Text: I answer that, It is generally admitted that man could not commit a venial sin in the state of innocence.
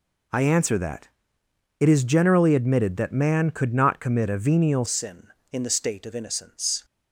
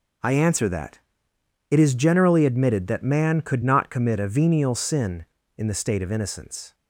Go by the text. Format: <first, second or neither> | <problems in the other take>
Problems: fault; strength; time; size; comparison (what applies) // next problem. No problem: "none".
second | changes voice at "sin"; from 4.8 s on; 2.0 s long